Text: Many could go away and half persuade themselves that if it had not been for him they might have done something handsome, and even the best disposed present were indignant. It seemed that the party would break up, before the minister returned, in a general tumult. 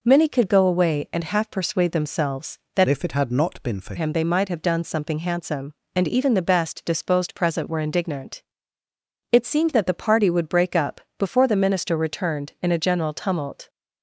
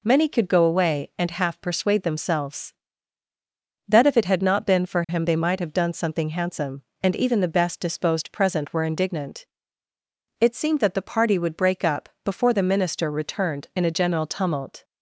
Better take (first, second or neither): second